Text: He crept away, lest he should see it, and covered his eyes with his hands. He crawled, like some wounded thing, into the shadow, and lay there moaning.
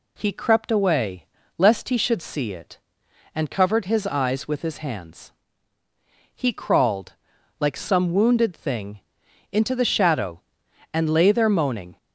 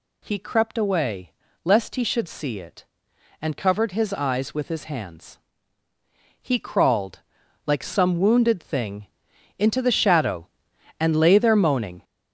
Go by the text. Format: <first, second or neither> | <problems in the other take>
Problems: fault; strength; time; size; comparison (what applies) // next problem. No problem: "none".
first | gets louder; strong; throughout; 8 dB